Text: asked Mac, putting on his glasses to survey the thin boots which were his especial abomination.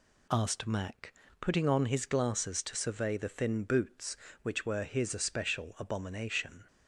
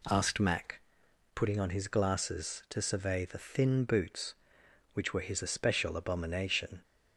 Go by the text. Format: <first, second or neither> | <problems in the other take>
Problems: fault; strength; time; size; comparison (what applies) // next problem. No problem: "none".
neither | none